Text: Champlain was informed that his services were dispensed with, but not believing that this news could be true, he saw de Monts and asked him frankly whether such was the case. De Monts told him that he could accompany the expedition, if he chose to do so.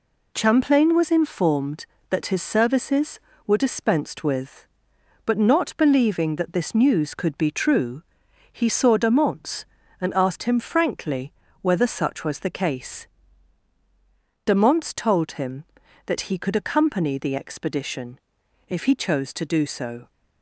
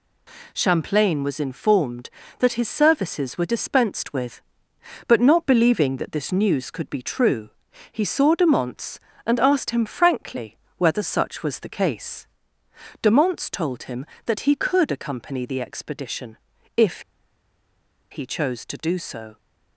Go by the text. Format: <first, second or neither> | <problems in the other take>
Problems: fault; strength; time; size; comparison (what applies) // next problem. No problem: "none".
first | pauses between "frankly" and "whether"; slight; at 10.5 s; 0.20 s long; slight in the first // pauses between "if" and "he"; at 17.0 s; 1.0 s long